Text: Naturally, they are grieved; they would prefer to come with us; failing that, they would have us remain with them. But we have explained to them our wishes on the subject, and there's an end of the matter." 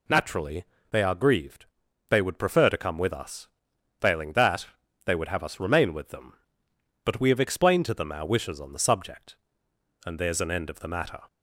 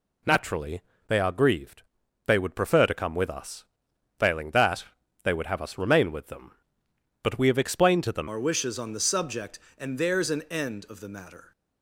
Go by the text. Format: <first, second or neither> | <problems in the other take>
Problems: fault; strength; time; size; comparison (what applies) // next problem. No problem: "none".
first | changes voice at "our"; from 8.2 s on; 3.3 s long